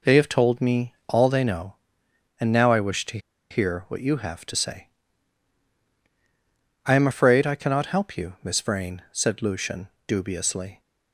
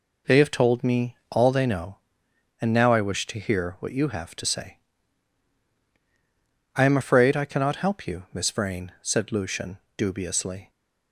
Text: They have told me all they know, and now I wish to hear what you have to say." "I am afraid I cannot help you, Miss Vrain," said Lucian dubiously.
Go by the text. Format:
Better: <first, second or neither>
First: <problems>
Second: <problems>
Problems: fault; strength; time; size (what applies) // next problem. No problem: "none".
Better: second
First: pauses between "to" and "hear"; slight; at 3.1 s; 0.32 s long // pauses between "Lucian" and "dubiously"; slight; at 9.8 s; 0.18 s long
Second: pauses between "Lucian" and "dubiously"; slight; at 9.7 s; 0.18 s long